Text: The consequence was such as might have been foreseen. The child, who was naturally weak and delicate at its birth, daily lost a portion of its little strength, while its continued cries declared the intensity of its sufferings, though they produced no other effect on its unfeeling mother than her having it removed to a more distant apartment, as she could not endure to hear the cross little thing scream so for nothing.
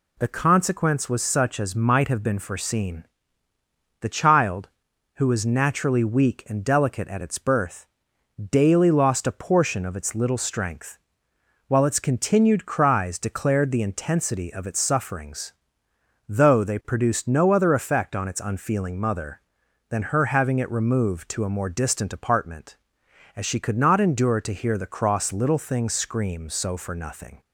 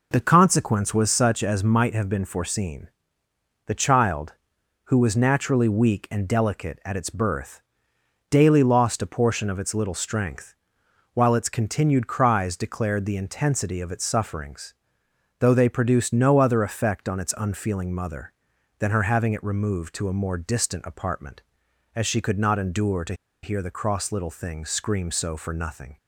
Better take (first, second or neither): first